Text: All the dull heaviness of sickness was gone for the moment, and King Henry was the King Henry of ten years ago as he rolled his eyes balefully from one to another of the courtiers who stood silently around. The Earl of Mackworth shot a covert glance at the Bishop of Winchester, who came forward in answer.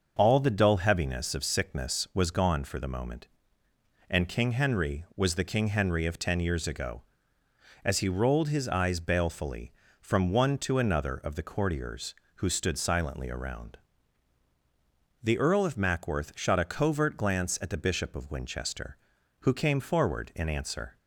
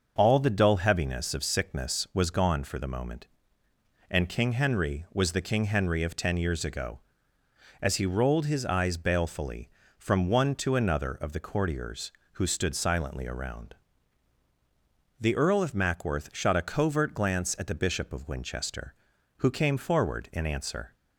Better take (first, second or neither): neither